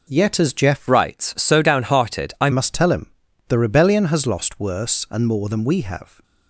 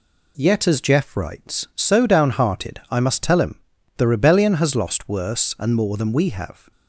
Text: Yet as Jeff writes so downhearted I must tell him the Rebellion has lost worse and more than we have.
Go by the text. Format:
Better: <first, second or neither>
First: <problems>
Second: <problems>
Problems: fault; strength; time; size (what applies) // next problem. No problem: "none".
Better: second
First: changes voice from "writes" to "I"; from 0.8 to 2.4 s; 1.6 s long // pauses between "him" and "the"; at 3.1 s; 0.38 s long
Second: pauses between "him" and "the"; at 3.5 s; 0.38 s long